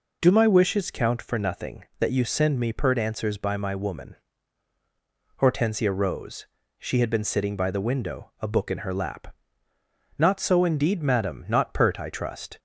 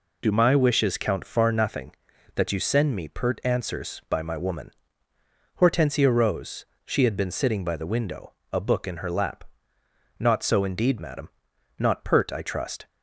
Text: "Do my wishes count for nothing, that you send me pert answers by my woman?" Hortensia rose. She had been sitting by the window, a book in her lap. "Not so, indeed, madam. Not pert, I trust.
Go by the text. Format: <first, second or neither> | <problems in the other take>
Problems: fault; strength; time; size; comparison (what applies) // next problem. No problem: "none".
first | says "far" for "for"; at 1.2 s